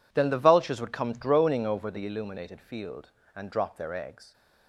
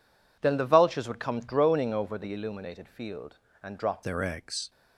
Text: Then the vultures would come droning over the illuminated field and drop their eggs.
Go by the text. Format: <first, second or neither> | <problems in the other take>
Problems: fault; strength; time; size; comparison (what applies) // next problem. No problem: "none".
first | changes voice at "their"; from 4.0 s on; 0.6 s long